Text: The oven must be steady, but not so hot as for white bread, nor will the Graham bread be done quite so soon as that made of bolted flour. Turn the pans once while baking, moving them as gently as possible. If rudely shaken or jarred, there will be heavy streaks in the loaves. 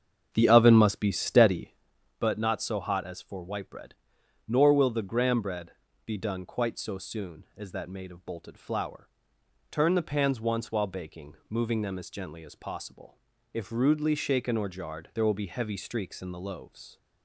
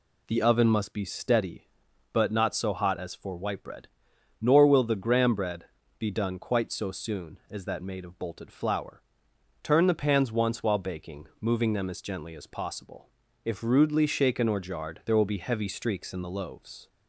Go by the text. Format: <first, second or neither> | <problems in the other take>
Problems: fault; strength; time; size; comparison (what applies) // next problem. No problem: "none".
second | starts louder than the rest; strong; until 1.8 s; 7.5 dB // pauses between "bread" and "be"; slight; at 5.7 s; 0.34 s long; slight in the second